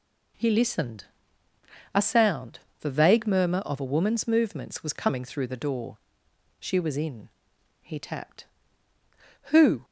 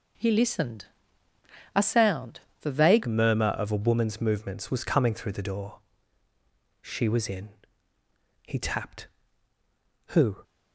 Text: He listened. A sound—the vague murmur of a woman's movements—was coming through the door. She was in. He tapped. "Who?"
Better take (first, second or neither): first